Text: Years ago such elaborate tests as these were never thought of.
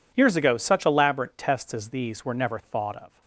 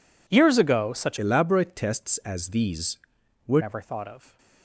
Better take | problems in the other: first | changes voice from "elaborate" to "were"; from 1.1 to 3.6 s; 2.5 s long

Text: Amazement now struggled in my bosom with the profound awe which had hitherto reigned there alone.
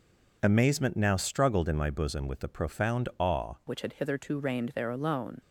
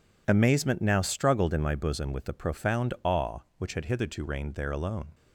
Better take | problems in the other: second | changes voice at "which"; from 3.6 s on; 1.8 s long

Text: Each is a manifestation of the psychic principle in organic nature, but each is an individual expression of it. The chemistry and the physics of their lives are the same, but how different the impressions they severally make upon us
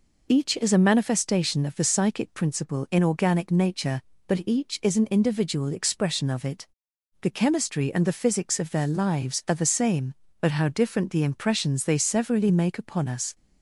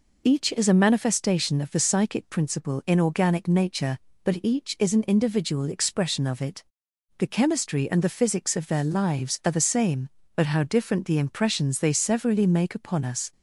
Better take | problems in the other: neither | none

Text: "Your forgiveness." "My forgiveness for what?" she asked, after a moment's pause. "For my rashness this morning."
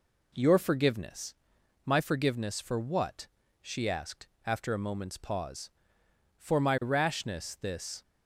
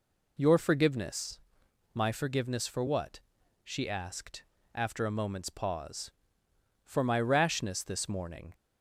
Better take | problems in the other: second | stops before "morning"; at 8.0 s

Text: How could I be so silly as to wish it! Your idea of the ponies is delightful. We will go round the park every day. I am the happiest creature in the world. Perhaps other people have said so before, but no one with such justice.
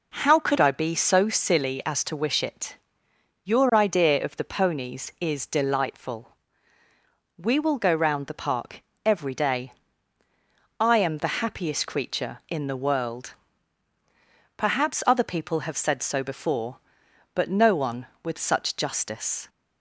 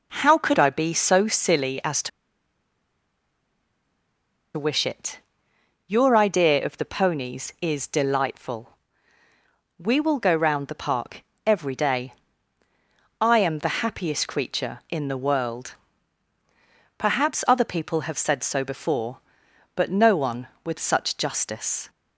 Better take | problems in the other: first | pauses between "to" and "wish"; strong; at 2.0 s; 2.4 s long // pauses between "park" and "every"; slight; at 11.2 s; 0.24 s long; slight in the first

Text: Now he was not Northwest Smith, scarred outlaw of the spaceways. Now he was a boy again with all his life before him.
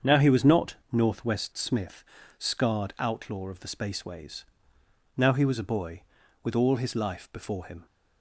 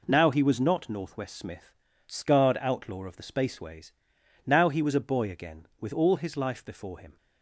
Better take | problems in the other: second | starts louder than the rest; strong; until 1.1 s; 7 dB // skips "again"; at 6.2 s

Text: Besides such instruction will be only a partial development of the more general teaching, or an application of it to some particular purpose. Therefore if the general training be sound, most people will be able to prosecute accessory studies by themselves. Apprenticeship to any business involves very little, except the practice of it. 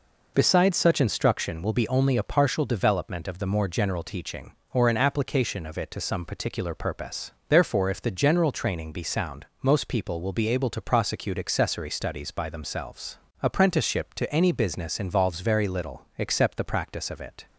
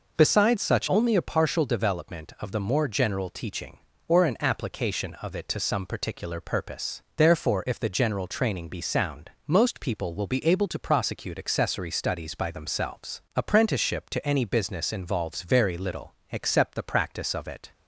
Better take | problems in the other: first | skips "instruction will be"; at 0.8 s

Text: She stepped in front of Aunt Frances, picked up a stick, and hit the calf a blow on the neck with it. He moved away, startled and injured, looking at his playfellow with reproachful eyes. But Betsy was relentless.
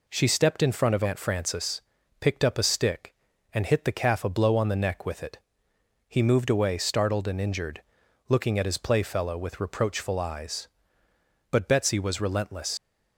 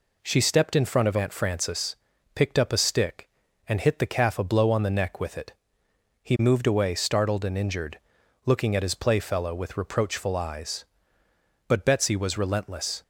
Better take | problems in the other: second | leaves "relentless" unfinished; at 12.7 s; 80 ms

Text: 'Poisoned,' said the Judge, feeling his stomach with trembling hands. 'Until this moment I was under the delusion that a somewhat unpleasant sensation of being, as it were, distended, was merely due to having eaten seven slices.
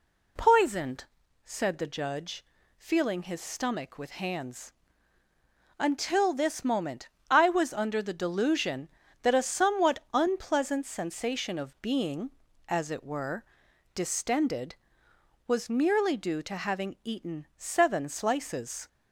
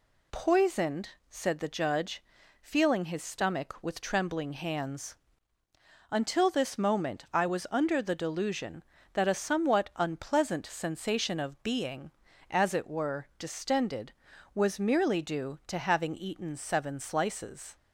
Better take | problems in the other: second | skips "trembling"; at 4.2 s // pauses between "moment" and "I"; slight; at 7.0 s; 0.22 s long

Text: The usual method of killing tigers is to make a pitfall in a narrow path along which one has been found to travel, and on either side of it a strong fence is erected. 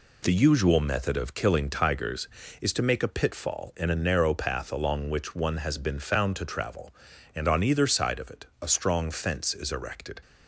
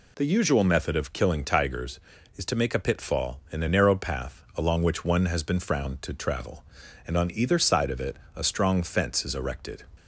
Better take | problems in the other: first | says "frowned" for "found"; at 5.5 s // pauses between "it" and "a"; slight; at 8.1 s; 0.18 s long; slight in the first

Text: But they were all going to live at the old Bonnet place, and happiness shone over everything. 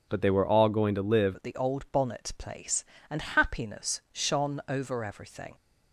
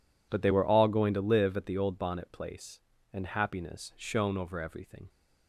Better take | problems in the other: second | changes voice at "at"; from 1.3 s on; 4.2 s long

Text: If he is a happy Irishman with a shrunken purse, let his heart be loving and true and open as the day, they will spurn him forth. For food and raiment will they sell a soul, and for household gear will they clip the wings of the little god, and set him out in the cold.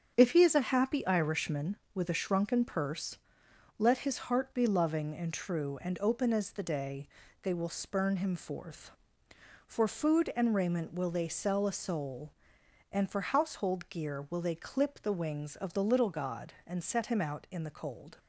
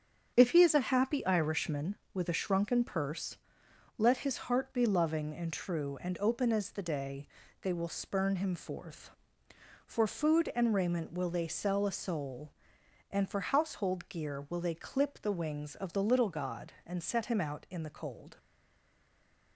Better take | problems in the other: first | starts louder than the rest; strong; until 1.3 s; 8 dB; strong in the first // stays silent after the last word; noticeable; from 18.3 s on; 1.2 s long

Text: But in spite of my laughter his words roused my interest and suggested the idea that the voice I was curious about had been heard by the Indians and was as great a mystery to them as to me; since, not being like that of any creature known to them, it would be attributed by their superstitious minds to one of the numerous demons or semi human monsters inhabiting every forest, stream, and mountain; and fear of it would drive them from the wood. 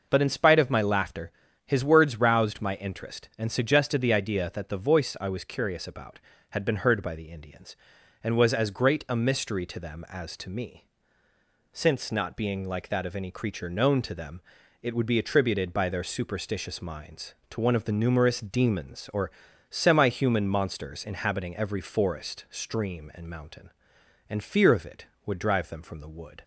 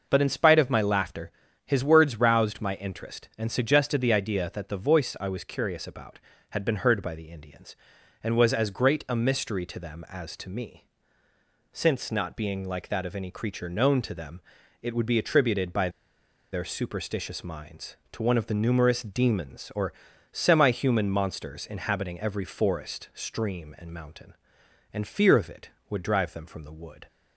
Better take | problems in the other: first | pauses between "laughter" and "his"; slight; at 1.2 s; 0.36 s long; slight in the first // pauses between "by" and "their"; noticeable; at 15.8 s; 0.62 s long // pauses between "or" and "semi"; at 19.9 s; 0.40 s long; also in the first

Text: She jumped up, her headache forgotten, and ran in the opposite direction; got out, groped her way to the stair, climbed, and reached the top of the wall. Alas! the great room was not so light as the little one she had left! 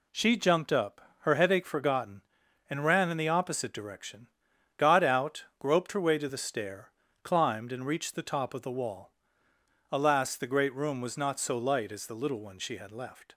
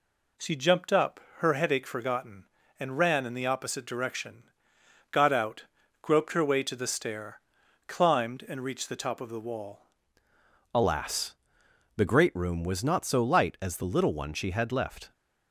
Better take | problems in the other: first | changes voice at "Alas"; from 10.7 s on; 4.4 s long

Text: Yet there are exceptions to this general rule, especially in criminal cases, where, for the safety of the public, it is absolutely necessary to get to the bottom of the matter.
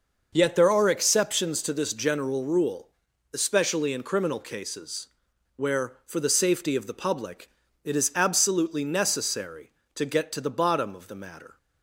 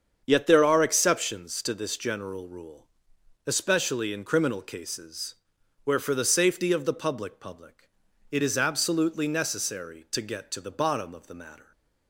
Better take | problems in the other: first | starts louder than the rest; strong; until 1.2 s; 7 dB // says "public" twice; at 7.4 s

